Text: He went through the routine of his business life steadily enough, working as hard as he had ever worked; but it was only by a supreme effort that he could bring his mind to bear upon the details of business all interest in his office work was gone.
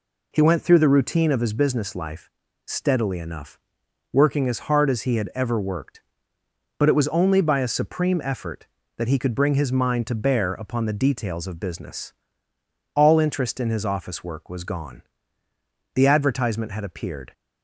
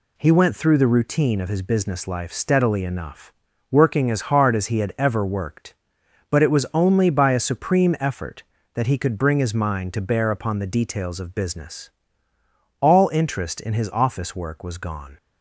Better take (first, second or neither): second